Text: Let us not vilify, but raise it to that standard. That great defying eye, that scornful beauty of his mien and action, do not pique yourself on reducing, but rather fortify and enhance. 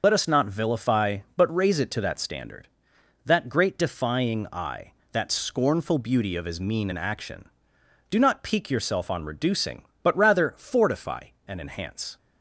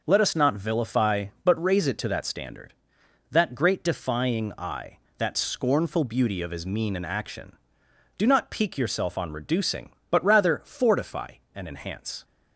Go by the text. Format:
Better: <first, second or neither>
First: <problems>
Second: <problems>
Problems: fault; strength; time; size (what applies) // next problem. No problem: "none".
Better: second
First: loses the start of "Let"; at 0.0 s; 75 ms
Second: none